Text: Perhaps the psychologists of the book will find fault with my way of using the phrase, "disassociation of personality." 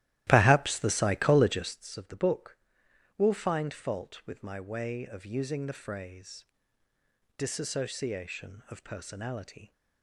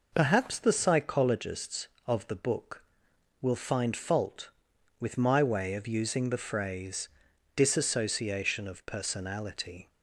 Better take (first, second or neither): second